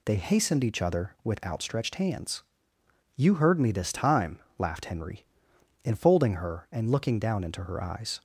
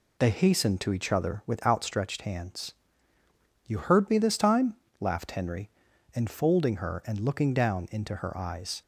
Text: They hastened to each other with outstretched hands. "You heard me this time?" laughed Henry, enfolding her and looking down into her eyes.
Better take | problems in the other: second | skips "to"; at 0.6 s

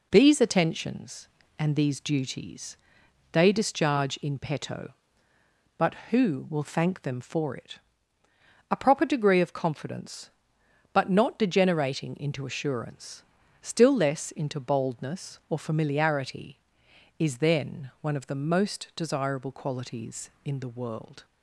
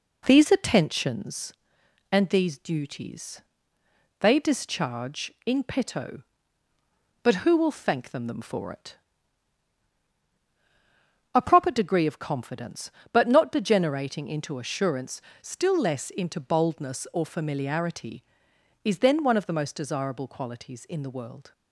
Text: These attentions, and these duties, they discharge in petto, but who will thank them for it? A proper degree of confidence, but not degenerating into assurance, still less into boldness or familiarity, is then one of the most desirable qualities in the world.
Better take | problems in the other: first | says "them" twice; at 8.2 s

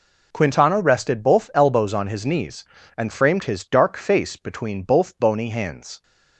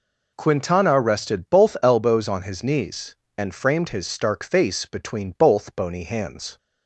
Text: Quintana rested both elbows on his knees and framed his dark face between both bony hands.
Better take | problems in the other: first | says "stark" for "dark"; at 4.0 s

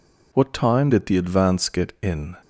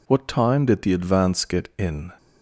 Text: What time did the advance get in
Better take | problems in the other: neither | none

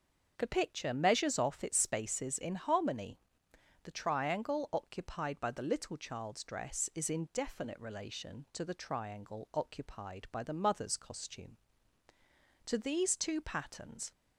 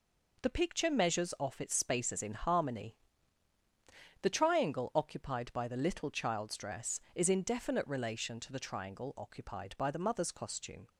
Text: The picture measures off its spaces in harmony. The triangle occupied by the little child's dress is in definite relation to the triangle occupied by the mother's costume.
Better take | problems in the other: second | starts louder than the rest; until 1.3 s; 6.5 dB // goes on to say "To these two patterns"; from 12.6 s on; 1.4 s long

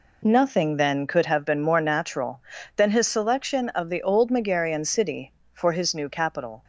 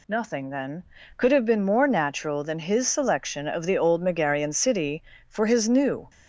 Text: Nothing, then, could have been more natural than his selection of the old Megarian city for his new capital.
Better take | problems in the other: first | stops before "capital"; at 6.0 s

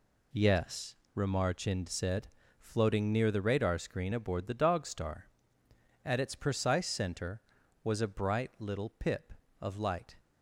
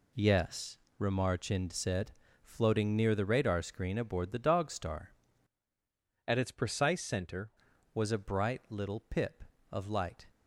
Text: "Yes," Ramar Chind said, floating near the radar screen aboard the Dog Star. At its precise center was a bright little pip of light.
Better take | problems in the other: first | changes voice from "At" to "center"; from 6.2 to 7.4 s; 1.2 s long

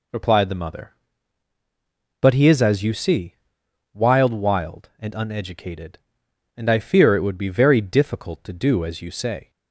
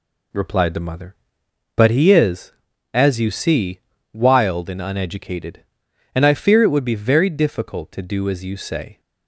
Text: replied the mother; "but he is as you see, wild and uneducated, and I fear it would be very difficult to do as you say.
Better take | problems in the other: second | says "wild" twice; at 4.3 s

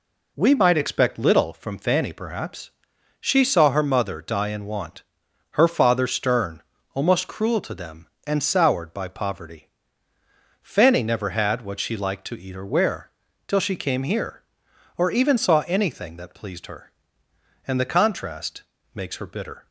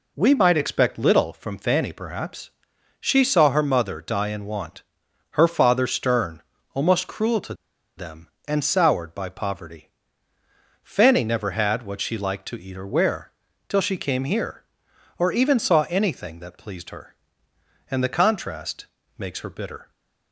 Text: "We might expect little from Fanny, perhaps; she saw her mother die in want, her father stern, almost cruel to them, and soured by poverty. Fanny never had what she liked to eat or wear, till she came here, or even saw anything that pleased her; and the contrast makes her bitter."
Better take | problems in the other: first | pauses between "to" and "them"; at 7.5 s; 0.44 s long // pauses between "contrast" and "makes"; slight; at 18.8 s; 0.32 s long; slight in the first

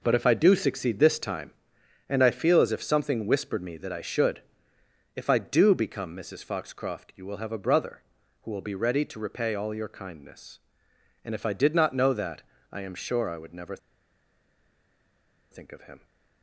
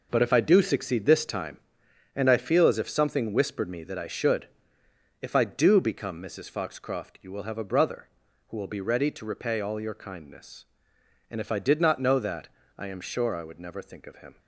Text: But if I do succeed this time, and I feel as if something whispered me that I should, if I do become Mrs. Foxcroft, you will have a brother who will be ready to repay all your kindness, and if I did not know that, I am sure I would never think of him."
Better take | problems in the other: second | pauses between "never" and "think"; strong; at 13.7 s; 1.7 s long

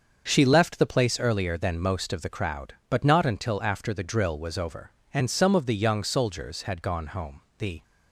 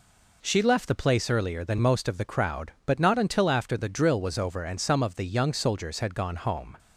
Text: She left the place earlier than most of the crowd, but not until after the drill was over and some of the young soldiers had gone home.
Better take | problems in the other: second | starts louder than the rest; until 1.2 s; 6.5 dB // goes on to say "The"; slight; from 7.5 s on; 0.24 s long

